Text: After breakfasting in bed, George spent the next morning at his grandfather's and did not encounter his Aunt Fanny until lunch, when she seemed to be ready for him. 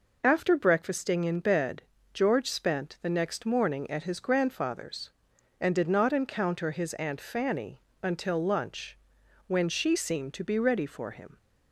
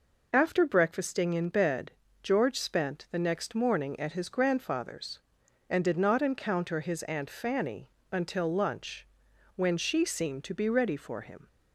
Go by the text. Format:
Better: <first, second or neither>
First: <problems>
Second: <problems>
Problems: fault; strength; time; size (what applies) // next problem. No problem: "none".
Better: neither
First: pauses between "Fanny" and "until"; slight; at 7.7 s; 0.24 s long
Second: pauses between "Fanny" and "until"; slight; at 7.8 s; 0.24 s long